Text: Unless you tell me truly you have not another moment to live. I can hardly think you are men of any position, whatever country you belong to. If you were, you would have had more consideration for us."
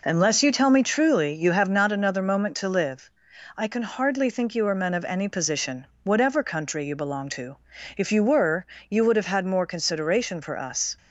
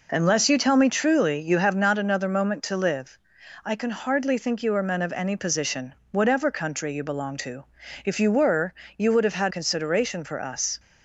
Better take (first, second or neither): first